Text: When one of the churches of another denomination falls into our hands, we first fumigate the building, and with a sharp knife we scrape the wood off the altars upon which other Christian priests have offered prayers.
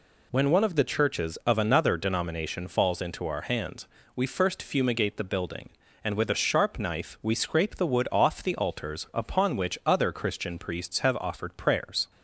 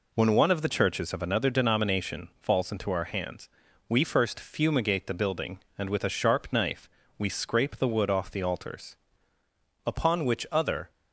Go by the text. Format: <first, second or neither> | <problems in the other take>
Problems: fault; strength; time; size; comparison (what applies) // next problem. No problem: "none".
first | pauses between "knife" and "we"; slight; at 6.8 s; 0.32 s long // pauses between "altars" and "upon"; noticeable; at 8.9 s; 0.88 s long // stops before "Christian priests have offered prayers"; at 10.9 s